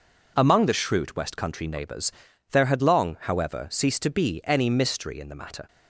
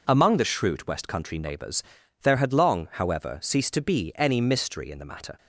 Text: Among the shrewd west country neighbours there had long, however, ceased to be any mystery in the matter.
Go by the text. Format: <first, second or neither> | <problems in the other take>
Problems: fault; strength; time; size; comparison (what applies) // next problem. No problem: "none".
neither | pauses between "neighbours" and "there"; the same in both